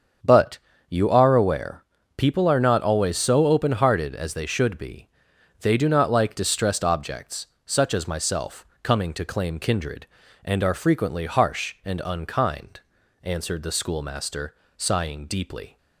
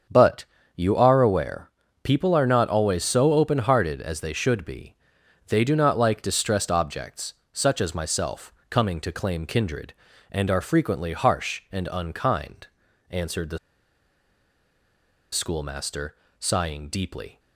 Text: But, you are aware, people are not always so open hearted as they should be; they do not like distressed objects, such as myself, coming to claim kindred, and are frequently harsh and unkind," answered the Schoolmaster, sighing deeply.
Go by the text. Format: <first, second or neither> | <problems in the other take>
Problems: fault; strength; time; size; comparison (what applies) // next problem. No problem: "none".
first | starts louder than the rest; strong; until 1.4 s; 7.5 dB; also in the first // pauses between "the" and "Schoolmaster"; strong; at 13.5 s; 1.7 s long